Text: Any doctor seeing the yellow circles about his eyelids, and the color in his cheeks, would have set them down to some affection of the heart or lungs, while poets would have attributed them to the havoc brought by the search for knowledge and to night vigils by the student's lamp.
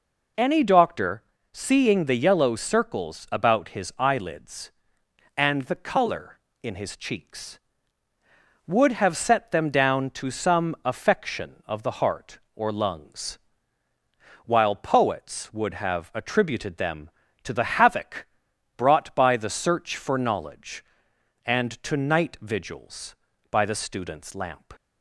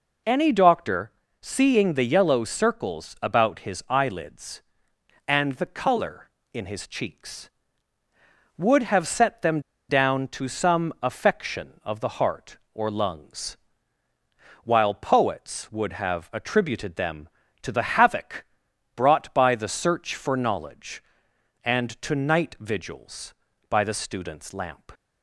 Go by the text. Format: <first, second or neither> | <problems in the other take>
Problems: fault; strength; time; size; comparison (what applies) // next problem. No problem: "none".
first | pauses between "doctor" and "seeing"; slight; at 1.0 s; 0.32 s long; slight in the first // pauses between "them" and "down"; slight; at 9.5 s; 0.29 s long // pauses between "havoc" and "brought"; noticeable; at 18.4 s; 0.50 s long; noticeable in the first